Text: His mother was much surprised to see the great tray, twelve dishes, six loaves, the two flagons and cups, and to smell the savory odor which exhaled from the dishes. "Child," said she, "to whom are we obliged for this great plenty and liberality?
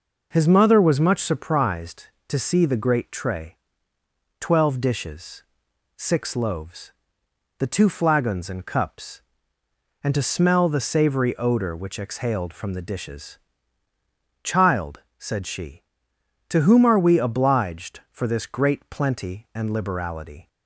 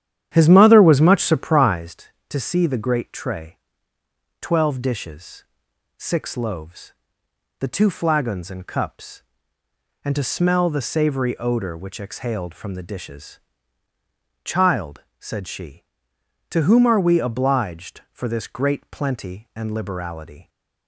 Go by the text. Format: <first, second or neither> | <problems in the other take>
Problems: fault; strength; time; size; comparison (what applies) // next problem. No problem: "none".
first | starts louder than the rest; strong; until 1.9 s; 10.5 dB